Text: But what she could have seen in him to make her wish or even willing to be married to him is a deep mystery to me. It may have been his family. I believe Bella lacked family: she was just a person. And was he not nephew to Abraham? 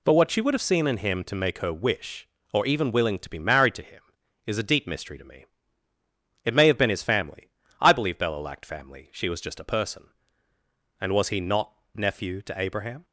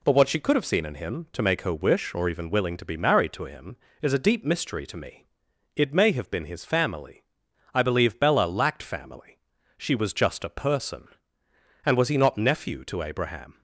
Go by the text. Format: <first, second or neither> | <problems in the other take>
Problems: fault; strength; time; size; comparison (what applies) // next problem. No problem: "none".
second | says "would" for "could"; at 0.4 s // pauses between "not" and "nephew"; slight; at 11.7 s; 0.22 s long